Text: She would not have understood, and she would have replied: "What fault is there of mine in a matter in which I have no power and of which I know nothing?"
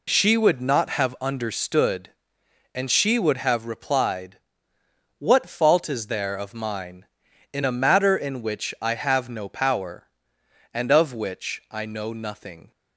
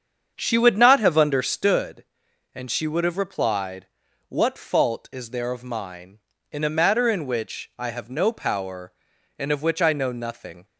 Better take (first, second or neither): first